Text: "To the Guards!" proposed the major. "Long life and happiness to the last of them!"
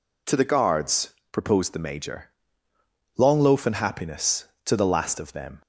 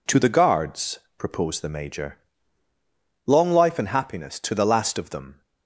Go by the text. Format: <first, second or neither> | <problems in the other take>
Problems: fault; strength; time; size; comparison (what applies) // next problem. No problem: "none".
second | says "loaf" for "life"; at 3.4 s